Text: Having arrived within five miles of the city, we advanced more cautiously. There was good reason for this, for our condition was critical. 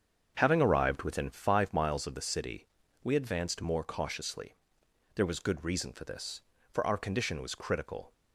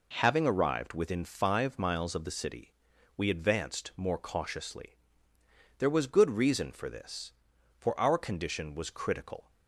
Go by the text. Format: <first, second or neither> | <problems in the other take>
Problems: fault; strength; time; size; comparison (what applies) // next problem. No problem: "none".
second | starts louder than the rest; strong; until 1.7 s; 7.5 dB